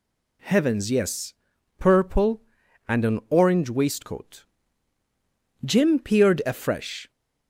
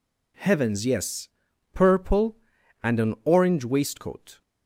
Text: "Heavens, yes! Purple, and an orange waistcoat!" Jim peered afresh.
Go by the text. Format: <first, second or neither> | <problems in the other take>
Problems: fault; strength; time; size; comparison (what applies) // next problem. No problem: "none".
first | stops before "Jim peered afresh"; at 4.4 s